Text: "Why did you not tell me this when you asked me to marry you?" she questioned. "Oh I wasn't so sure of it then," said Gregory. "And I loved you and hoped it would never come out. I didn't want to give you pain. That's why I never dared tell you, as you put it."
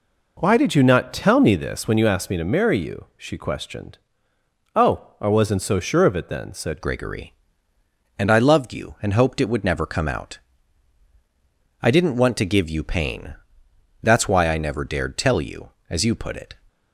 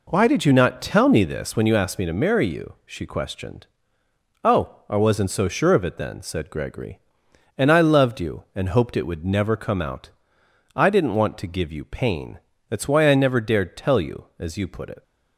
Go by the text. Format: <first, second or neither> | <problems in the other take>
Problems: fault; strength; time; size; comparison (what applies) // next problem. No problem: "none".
second | changes voice at "Gregory"; from 6.8 s on; 9.7 s long